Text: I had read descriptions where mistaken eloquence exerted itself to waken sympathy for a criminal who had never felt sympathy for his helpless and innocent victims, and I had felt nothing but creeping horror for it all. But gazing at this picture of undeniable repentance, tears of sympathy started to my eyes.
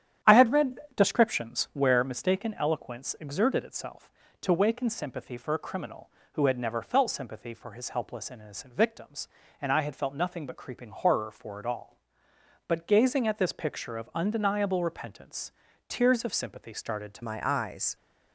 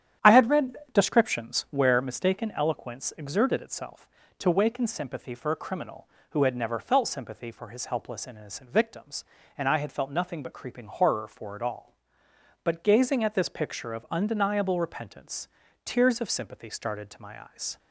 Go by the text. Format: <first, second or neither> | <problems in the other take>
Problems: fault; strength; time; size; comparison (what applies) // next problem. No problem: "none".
second | starts louder than the rest; strong; until 1.4 s; 10 dB; strong in the second // pauses between "read" and "descriptions"; slight; at 0.7 s; 0.16 s long; slight in the second // changes voice at "my"; from 17.2 s on; 0.7 s long